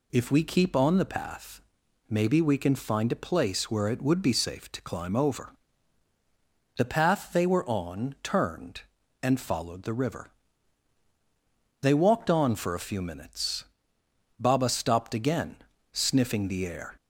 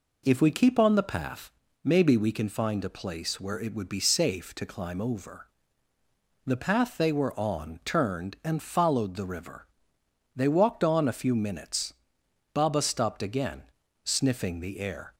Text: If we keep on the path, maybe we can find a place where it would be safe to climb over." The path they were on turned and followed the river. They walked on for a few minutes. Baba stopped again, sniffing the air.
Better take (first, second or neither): first